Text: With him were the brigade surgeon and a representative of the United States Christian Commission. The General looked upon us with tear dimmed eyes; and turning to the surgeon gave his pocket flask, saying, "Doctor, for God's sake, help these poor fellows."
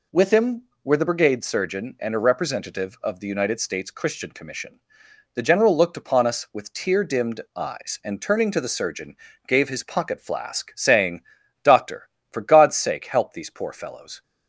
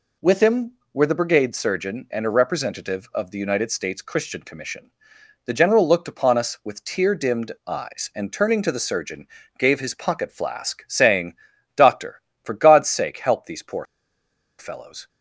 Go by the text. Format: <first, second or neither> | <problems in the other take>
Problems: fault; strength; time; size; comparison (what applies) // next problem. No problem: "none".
first | pauses between "dimmed" and "eyes"; slight; at 7.5 s; 0.16 s long; slight in the first // pauses between "surgeon" and "gave"; slight; at 9.2 s; 0.30 s long; slight in the first // pauses between "poor" and "fellows"; noticeable; at 13.8 s; 0.74 s long